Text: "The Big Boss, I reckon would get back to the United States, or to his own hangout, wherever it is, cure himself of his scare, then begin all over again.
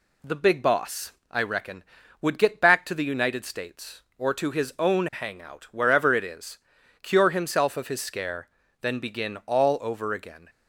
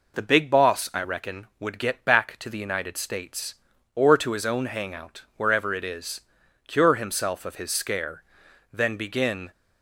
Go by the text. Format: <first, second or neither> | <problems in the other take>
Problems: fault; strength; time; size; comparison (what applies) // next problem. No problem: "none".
first | stops before "all over again"; at 9.5 s